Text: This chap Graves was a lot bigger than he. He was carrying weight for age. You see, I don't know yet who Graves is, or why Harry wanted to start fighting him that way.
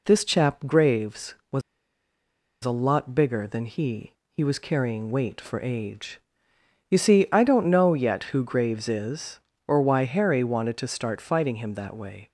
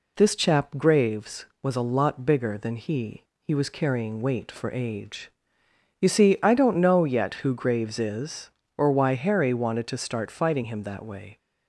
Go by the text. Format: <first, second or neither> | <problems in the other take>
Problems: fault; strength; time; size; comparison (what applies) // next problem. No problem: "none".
second | pauses between "was" and "a"; at 1.6 s; 1.0 s long